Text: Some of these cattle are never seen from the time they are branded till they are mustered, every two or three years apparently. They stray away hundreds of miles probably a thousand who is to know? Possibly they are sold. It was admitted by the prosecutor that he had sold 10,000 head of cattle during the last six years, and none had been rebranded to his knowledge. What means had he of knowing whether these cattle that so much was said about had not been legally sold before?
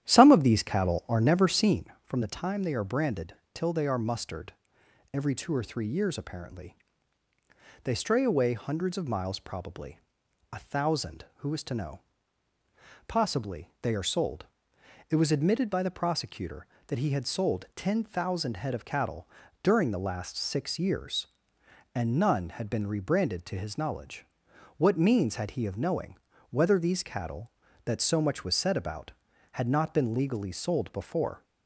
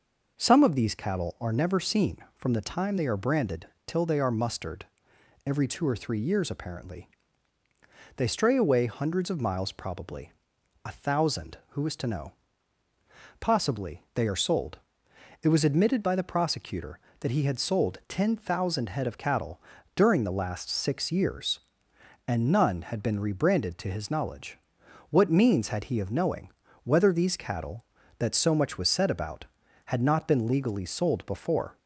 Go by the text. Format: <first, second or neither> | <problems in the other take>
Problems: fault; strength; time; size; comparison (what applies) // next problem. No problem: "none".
second | starts louder than the rest; strong; until 1.9 s; 11.5 dB // pauses between "branded" and "till"; slight; at 3.3 s; 0.18 s long; slight in the second // pauses between "probably" and "a"; noticeable; at 9.9 s; 0.54 s long; noticeable in the second // pauses between "cattle" and "during"; slight; at 19.2 s; 0.34 s long; slight in the second // pauses between "knowing" and "whether"; slight; at 26.1 s; 0.34 s long; slight in the second